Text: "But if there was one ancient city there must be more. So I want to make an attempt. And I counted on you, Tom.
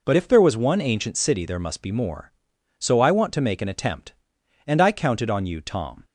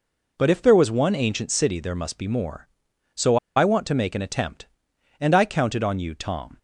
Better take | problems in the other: first | pauses between "So" and "I"; slight; at 3.3 s; 0.19 s long

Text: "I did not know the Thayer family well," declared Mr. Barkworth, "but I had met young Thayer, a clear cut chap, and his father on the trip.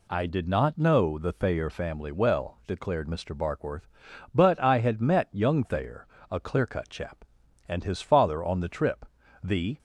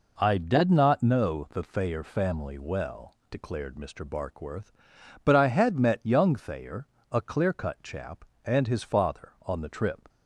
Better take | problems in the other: second | goes on to say "The"; slight; from 9.4 s on; 0.36 s long

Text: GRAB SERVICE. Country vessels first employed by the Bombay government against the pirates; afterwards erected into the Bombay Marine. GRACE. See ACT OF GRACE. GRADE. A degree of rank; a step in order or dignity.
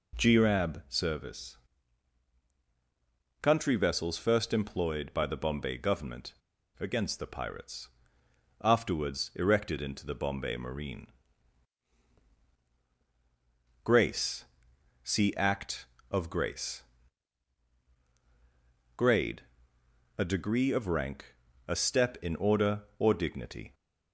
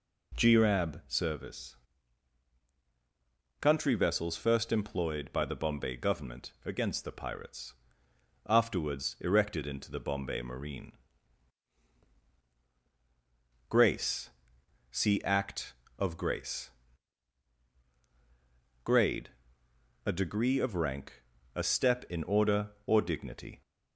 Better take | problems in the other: second | pauses between "government" and "against"; at 6.3 s; 0.45 s long

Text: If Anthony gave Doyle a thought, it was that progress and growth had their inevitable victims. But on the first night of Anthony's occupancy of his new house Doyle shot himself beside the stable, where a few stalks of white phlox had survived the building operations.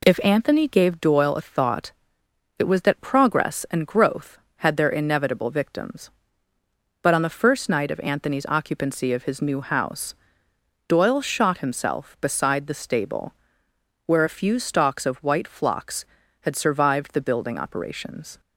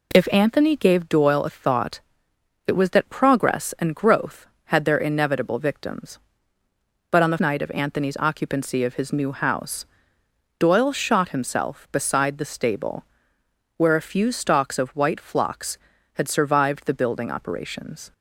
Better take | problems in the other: first | skips "first"; at 7.3 s // pauses between "house" and "Doyle"; noticeable; at 9.8 s; 0.76 s long; noticeable in the first

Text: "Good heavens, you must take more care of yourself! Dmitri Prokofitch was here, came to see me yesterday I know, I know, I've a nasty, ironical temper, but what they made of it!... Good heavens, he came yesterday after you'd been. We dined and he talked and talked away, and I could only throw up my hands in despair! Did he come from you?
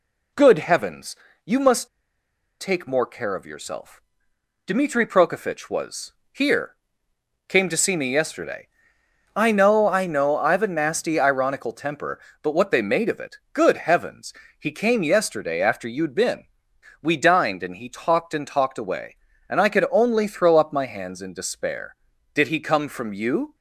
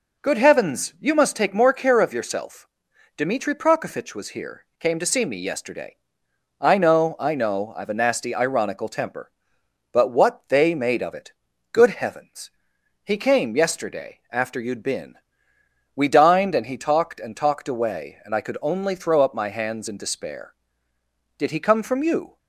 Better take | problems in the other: second | pauses between "must" and "take"; noticeable; at 1.8 s; 0.72 s long // pauses between "was" and "here"; slight; at 6.1 s; 0.20 s long // pauses between "yesterday" and "I"; noticeable; at 8.6 s; 0.66 s long; noticeable in the second

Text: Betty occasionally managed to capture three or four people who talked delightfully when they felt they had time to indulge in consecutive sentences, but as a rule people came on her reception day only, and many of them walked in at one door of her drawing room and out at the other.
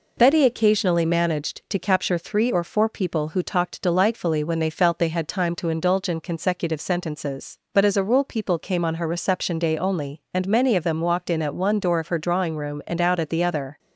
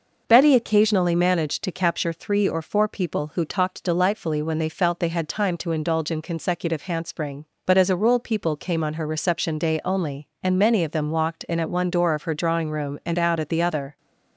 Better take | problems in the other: first | says "handspring" for "sentences"; at 6.8 s

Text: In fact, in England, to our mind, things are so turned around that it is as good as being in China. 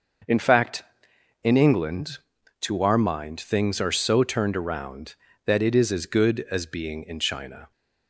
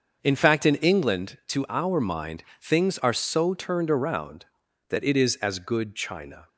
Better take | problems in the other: first | starts louder than the rest; until 1.2 s; 6.5 dB; also in the first // skips "as being in"; at 5.9 s

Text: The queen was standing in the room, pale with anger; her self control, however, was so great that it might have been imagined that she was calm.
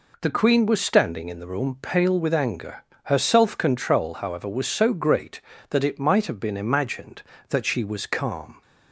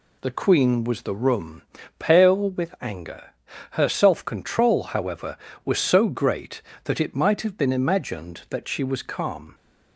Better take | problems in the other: first | skips "standing in"; at 1.0 s

